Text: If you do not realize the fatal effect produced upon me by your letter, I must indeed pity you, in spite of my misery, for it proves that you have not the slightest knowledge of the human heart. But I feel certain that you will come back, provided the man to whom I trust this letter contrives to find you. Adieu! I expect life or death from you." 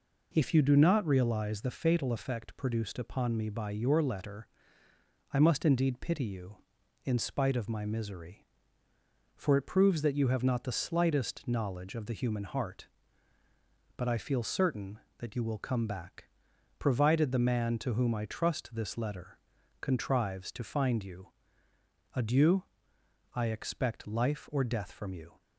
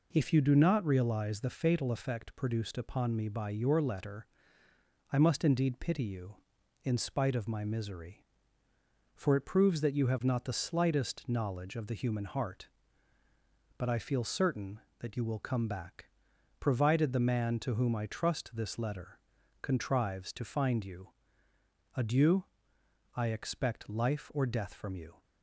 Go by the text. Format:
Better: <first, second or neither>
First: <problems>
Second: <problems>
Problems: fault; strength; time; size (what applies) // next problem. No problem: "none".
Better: neither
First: pauses between "letter" and "contrives"; noticeable; at 19.3 s; 0.46 s long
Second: pauses between "letter" and "contrives"; noticeable; at 19.1 s; 0.46 s long